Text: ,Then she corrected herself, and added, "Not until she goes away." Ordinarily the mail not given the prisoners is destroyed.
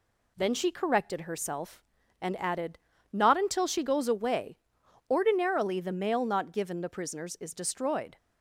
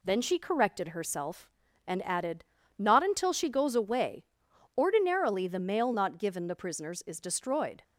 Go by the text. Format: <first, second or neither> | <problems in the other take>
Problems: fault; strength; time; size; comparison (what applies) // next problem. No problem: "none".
neither | none